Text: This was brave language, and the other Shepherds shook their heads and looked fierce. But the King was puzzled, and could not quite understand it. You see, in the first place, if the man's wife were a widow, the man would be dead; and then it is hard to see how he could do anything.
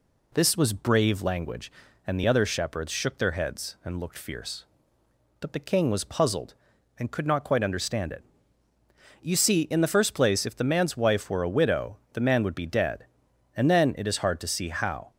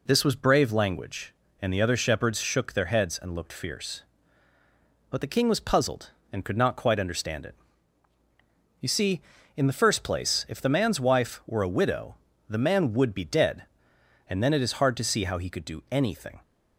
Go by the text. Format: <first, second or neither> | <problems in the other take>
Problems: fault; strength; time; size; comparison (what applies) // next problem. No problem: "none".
second | stops before "he could do anything"; at 15.1 s